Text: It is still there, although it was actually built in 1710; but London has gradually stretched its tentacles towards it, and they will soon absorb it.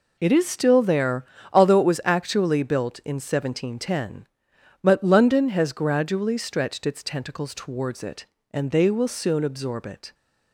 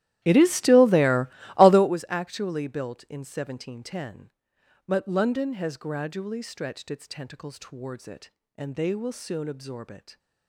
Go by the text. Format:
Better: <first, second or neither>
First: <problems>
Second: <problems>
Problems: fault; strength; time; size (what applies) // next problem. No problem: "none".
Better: first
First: none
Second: starts louder than the rest; strong; until 1.9 s; 13.5 dB